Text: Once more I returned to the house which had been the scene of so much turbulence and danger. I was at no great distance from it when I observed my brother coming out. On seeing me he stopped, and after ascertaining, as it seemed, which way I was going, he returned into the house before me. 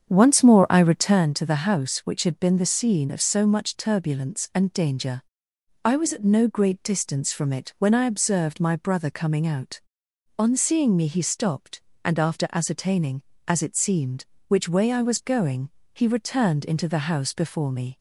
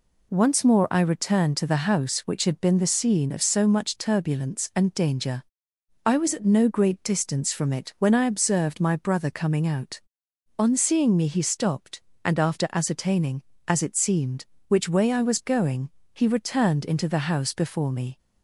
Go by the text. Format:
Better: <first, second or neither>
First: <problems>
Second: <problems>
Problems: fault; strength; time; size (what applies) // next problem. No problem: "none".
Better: second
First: starts louder than the rest; strong; until 1.3 s; 7.5 dB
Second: none